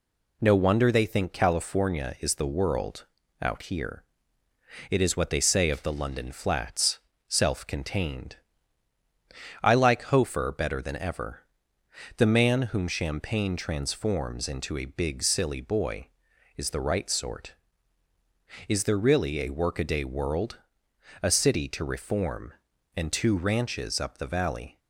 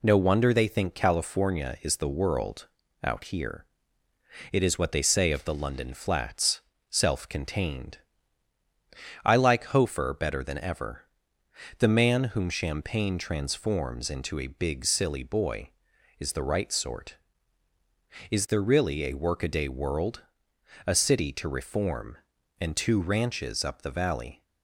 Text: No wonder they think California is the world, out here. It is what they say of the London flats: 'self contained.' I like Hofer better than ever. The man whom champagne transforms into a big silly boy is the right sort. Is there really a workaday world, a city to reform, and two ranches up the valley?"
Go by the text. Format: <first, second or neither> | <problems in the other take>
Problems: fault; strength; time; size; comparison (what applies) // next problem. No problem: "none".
neither | none